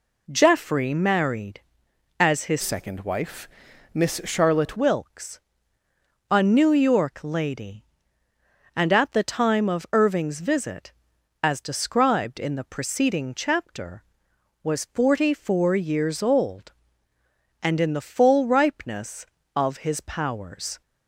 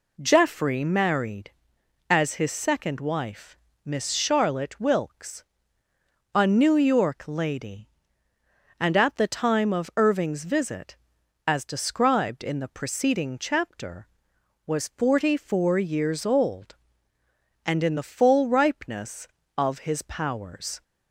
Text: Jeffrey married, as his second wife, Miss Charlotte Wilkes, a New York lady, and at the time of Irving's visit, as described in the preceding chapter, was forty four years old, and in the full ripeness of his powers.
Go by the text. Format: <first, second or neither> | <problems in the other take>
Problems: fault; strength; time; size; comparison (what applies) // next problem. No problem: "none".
second | changes voice from "second" to "Charlotte"; from 2.6 to 4.7 s; 2.1 s long